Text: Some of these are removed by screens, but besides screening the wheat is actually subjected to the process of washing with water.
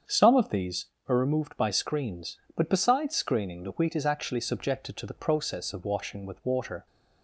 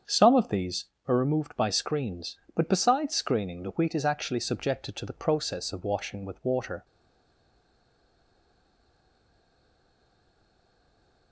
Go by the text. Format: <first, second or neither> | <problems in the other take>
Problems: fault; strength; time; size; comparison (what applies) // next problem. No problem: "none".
first | starts louder than the rest; strong; until 1.2 s; 7.5 dB; strong in the first // stays silent after the last word; strong; from 6.8 s on; 4.5 s long